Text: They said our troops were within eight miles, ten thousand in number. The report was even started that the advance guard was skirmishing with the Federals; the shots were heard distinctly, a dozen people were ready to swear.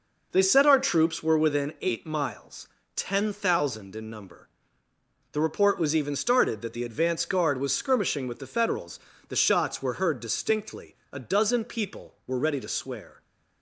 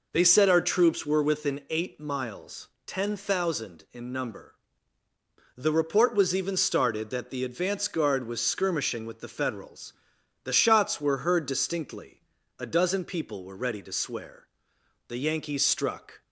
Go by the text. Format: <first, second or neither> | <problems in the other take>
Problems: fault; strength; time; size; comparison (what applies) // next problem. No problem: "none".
first | goes on to say "The Yankees struck"; noticeable; from 15.0 s on; 1.1 s long